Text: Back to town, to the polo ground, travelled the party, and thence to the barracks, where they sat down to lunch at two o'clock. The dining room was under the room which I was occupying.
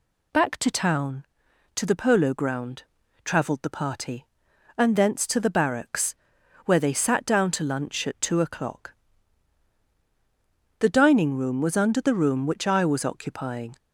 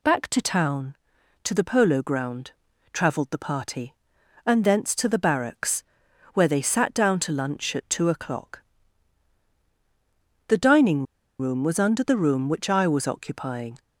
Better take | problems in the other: first | pauses between "dining" and "room"; slight; at 11.0 s; 0.34 s long

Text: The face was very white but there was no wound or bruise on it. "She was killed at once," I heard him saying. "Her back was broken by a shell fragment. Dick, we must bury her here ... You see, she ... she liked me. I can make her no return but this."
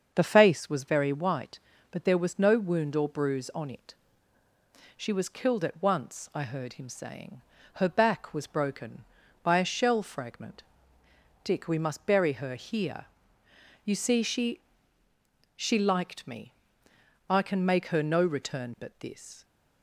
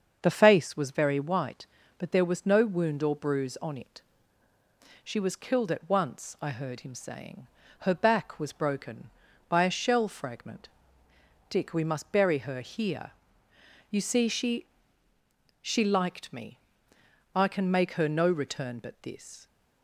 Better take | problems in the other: neither | starts louder than the rest; the same in both

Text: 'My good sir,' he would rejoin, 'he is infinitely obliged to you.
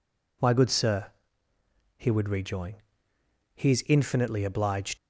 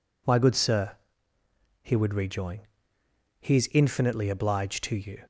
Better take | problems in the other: second | stops before "to you"; at 4.9 s

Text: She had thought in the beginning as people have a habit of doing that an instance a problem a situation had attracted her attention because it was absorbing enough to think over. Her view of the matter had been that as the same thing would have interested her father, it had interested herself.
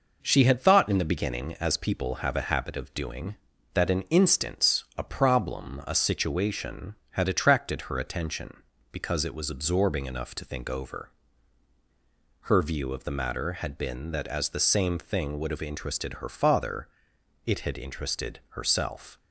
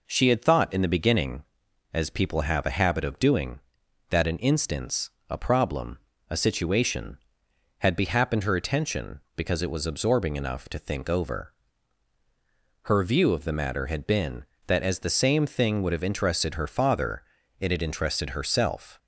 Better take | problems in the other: first | pauses between "instance" and "a"; slight; at 5.1 s; 0.18 s long // pauses between "problem" and "a"; slight; at 5.9 s; 0.32 s long // says "behappened" for "attracted"; at 7.9 s

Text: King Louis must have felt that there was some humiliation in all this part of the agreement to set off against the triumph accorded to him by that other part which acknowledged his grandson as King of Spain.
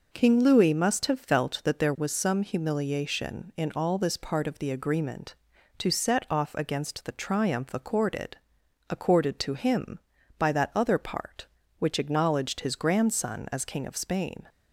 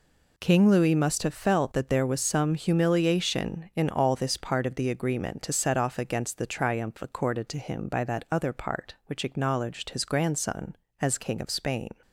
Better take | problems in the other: second | says "accorded" twice; at 8.8 s

